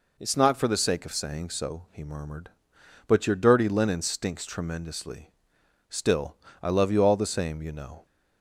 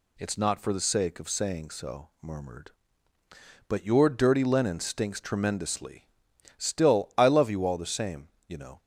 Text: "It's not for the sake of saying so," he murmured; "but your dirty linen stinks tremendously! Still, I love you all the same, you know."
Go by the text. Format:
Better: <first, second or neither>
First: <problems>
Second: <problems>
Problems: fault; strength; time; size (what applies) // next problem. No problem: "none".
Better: first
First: none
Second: skips "he"; at 2.1 s